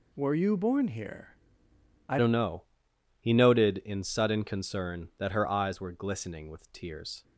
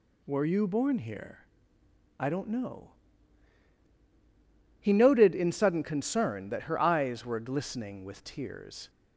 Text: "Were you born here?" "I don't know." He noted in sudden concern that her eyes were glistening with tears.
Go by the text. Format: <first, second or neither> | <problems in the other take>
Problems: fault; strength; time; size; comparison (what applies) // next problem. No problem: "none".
second | changes voice at "don't"; from 2.1 s on; 5.1 s long